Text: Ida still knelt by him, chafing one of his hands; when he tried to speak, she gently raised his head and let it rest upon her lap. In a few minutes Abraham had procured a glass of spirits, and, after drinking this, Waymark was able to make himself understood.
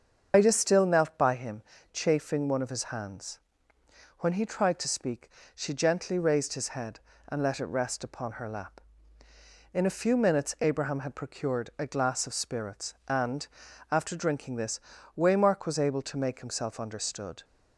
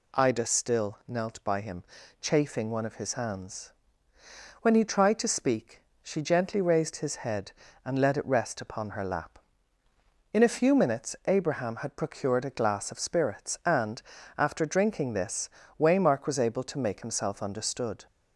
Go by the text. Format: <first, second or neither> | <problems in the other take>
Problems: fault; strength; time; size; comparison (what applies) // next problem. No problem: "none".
second | loses the start of "Ida"; at 0.3 s; 125 ms // starts louder than the rest; until 1.3 s; 7 dB